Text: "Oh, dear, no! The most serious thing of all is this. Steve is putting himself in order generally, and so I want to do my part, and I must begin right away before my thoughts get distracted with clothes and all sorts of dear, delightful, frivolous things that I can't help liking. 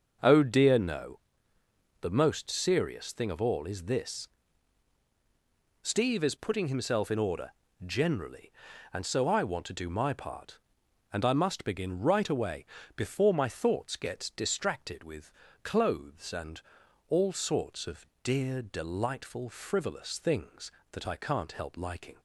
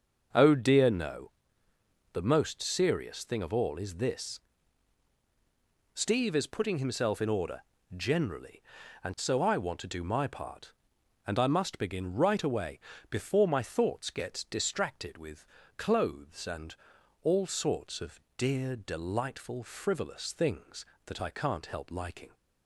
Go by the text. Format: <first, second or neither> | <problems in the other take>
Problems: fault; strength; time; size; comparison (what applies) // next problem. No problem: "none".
neither | starts louder than the rest; the same in both // pauses between "order" and "generally"; slight; the same in both // pauses between "away" and "before"; slight; the same in both // pauses between "with" and "clothes"; slight; the same in both // pauses between "and" and "all"; noticeable; the same in both // pauses between "of" and "dear"; slight; the same in both